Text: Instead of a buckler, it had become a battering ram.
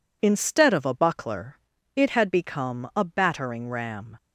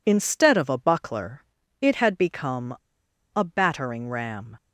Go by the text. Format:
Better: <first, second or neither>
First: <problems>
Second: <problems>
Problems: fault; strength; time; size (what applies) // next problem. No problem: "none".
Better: first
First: none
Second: pauses between "become" and "a"; noticeable; at 2.7 s; 0.61 s long